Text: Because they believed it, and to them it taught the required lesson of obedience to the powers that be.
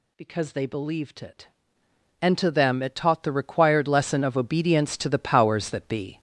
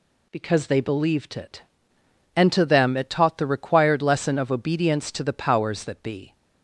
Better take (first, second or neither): second